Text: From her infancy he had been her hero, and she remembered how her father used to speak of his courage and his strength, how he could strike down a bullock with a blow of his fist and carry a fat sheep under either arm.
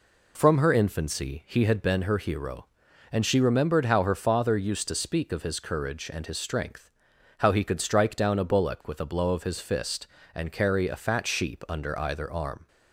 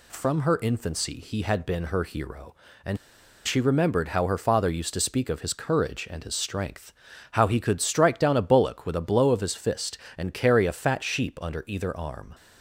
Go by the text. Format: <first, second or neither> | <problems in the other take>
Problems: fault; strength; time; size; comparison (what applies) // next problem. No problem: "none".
first | pauses between "and" and "she"; noticeable; at 2.9 s; 0.49 s long